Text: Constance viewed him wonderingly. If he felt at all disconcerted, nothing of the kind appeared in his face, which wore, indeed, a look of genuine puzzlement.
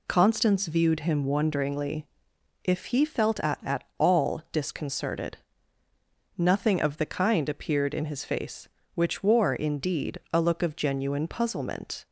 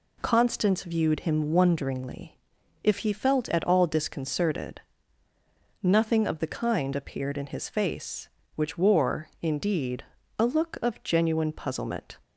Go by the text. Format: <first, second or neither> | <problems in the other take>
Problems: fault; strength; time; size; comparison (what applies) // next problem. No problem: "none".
second | says "at" twice; at 3.6 s